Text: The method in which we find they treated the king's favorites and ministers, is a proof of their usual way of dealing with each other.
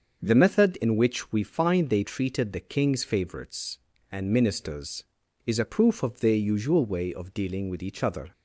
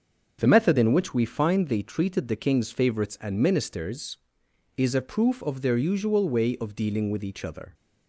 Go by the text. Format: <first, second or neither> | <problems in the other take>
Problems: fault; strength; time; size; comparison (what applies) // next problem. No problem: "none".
neither | starts louder than the rest; the same in both